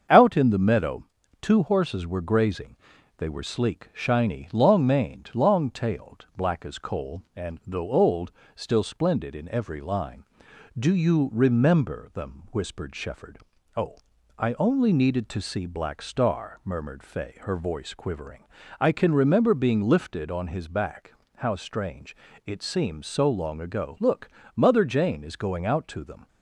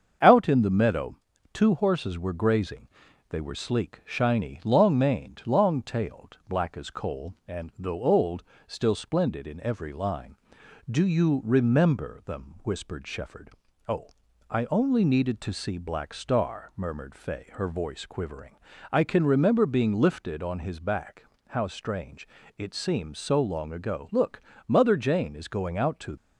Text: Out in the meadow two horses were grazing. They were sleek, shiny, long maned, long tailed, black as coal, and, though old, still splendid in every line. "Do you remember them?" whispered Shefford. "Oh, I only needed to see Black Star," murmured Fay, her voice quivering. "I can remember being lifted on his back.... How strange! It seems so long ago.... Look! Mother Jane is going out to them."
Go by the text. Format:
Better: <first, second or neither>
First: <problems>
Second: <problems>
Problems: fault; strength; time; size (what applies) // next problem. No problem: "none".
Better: first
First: starts louder than the rest; strong; until 1.4 s; 7 dB // pauses between "meadow" and "two"; at 1.0 s; 0.38 s long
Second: starts louder than the rest; strong; until 1.6 s; 7 dB // pauses between "meadow" and "two"; at 1.1 s; 0.38 s long // stops before "them"; at 26.1 s